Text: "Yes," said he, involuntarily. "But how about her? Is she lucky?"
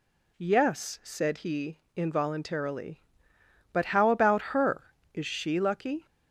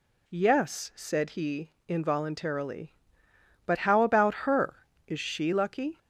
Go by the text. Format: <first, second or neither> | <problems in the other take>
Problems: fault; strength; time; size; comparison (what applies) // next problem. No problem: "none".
neither | none